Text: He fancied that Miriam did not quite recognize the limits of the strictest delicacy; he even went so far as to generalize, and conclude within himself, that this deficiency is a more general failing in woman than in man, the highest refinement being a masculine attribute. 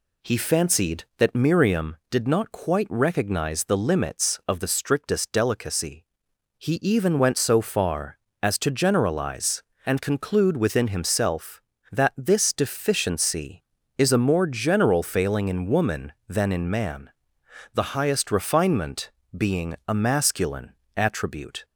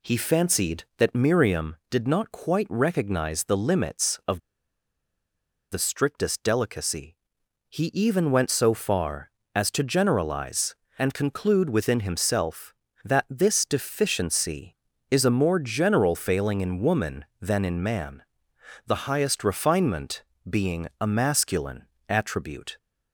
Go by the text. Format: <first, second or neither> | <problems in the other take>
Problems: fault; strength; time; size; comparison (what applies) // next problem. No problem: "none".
first | pauses between "of" and "the"; strong; at 4.3 s; 1.3 s long // pauses between "refinement" and "being"; slight; at 20.2 s; 0.24 s long; slight in the first // pauses between "masculine" and "attribute"; slight; at 21.8 s; 0.22 s long; slight in the first